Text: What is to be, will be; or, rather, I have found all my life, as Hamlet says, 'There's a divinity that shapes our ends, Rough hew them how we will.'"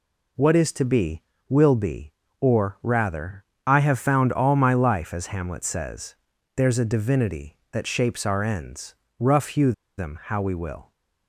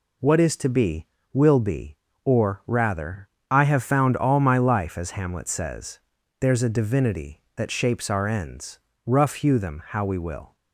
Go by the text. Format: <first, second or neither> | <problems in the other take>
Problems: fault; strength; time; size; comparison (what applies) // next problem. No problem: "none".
second | pauses between "hew" and "them"; slight; at 9.7 s; 0.25 s long